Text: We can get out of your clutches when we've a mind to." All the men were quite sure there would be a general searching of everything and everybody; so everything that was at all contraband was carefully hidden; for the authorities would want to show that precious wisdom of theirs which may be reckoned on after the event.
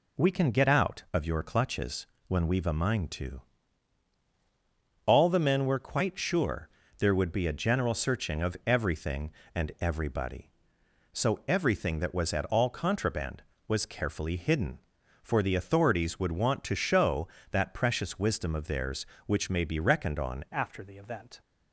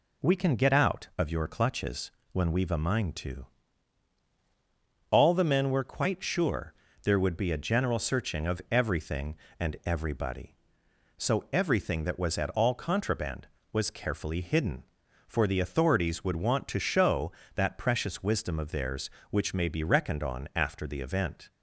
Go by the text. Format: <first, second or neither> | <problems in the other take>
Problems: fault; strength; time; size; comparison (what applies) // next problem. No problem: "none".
second | pauses between "clutches" and "when"; slight; at 2.0 s; 0.22 s long; slight in the second // pauses between "sure" and "there"; slight; at 6.6 s; 0.30 s long; slight in the second // changes voice at "after"; from 20.5 s on; 0.9 s long